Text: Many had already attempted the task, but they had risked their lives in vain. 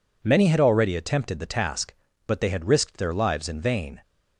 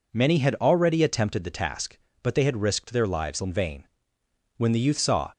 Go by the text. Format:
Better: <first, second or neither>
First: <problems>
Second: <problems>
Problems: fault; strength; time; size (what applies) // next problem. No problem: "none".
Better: first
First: none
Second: goes on to say "When the Youth saw"; noticeable; from 4.5 s on; 0.76 s long